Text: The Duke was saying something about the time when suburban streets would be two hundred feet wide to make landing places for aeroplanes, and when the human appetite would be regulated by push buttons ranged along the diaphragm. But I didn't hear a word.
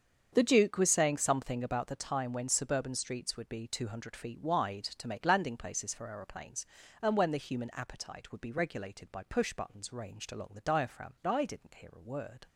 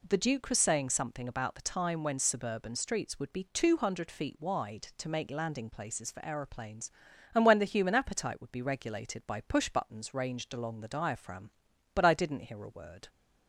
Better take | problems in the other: second | starts louder than the rest; strong; until 1.3 s; 7 dB // skips "But"; at 11.1 s

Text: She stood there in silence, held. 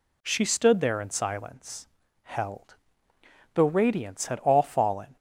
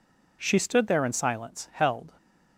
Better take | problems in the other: second | goes on to say "The radiance had all fallen"; from 3.5 s on; 1.6 s long

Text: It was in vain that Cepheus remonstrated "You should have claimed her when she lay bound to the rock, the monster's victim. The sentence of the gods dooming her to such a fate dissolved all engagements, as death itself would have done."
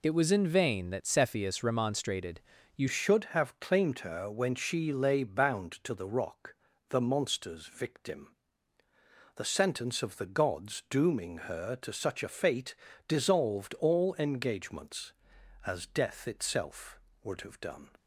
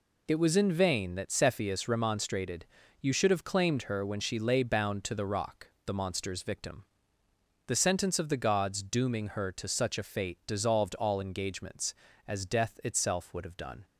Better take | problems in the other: second | pauses between "remonstrated" and "You"; slight; at 2.4 s; 0.34 s long; slight in the second // changes voice at "should"; from 2.8 s on; 15.0 s long // pauses between "fate" and "dissolved"; slight; at 12.7 s; 0.34 s long

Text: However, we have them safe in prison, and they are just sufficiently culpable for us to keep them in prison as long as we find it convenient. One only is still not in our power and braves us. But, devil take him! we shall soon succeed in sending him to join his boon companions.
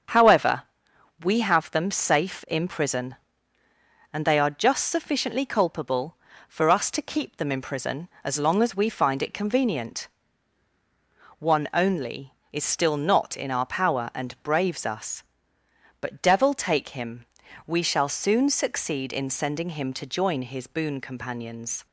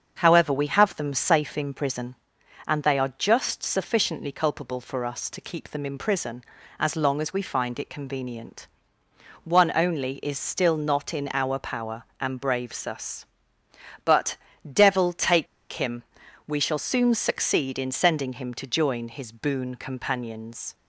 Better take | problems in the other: first | starts louder than the rest; until 1.1 s; 6.5 dB; strong in the first // pauses between "take" and "him"; slight; at 15.4 s; 0.25 s long

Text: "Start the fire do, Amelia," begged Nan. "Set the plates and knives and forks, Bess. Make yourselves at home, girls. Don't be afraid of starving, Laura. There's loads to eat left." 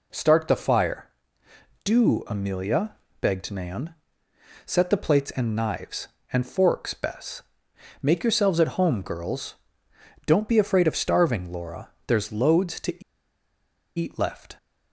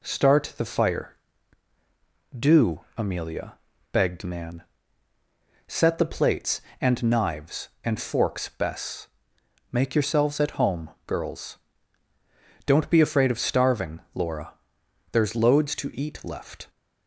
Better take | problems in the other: second | pauses between "to" and "eat"; noticeable; at 13.0 s; 0.96 s long

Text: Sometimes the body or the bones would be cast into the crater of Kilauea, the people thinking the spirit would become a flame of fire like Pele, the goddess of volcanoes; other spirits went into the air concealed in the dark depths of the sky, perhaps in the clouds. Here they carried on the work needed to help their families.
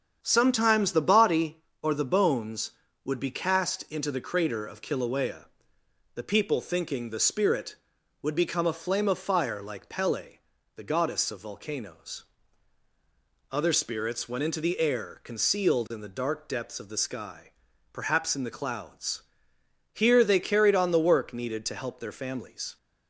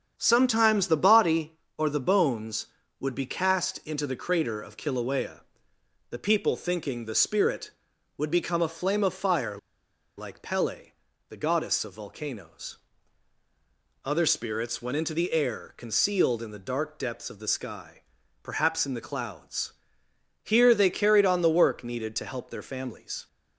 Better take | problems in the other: first | starts louder than the rest; strong; until 1.1 s; 8 dB; strong in the first // pauses between "fire" and "like"; noticeable; at 9.5 s; 0.62 s long

